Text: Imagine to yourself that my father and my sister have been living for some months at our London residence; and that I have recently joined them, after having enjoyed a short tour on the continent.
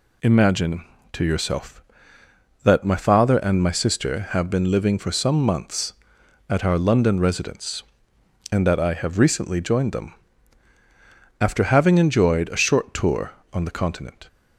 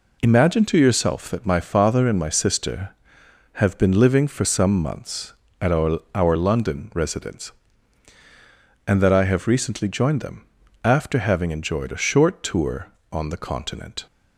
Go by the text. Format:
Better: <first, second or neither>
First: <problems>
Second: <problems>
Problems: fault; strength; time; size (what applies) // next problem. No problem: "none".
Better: first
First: none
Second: says "our" twice; at 6.1 s